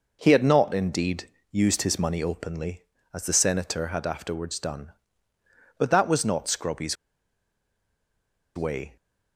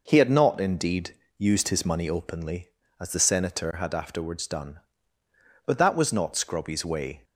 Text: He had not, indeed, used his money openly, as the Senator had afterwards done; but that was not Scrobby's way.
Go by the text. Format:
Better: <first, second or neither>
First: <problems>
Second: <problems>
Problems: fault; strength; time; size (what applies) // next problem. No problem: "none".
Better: second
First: pauses between "Scrobby's" and "way"; strong; at 6.9 s; 1.6 s long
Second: none